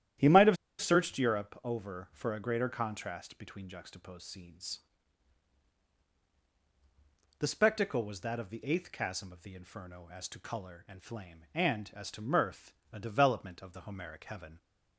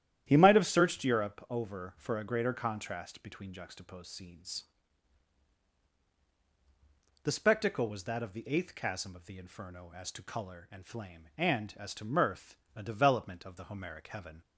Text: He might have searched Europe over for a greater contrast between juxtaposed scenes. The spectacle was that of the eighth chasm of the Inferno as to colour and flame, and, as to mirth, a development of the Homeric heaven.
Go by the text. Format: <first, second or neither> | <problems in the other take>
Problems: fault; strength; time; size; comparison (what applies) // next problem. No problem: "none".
second | starts louder than the rest; strong; until 1.4 s; 11.5 dB; strong in the second // pauses between "have" and "searched"; slight; at 0.5 s; 0.23 s long